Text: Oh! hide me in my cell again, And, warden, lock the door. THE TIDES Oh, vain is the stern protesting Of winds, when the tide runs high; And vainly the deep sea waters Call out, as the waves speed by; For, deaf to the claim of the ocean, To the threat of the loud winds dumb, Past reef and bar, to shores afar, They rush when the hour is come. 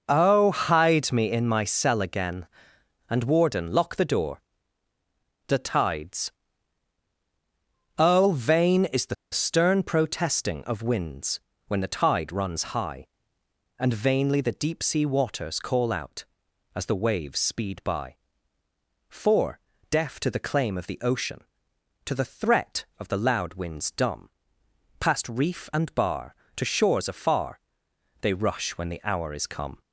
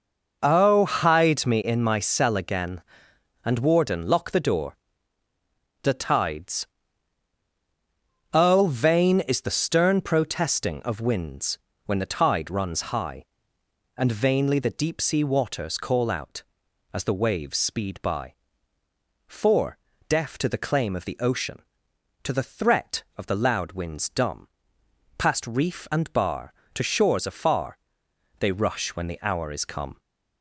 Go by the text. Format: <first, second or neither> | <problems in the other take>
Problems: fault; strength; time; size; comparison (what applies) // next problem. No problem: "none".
second | pauses between "TIDES" and "Oh"; strong; at 6.3 s; 1.6 s long; strong in the second // pauses between "the" and "stern"; slight; at 9.1 s; 0.17 s long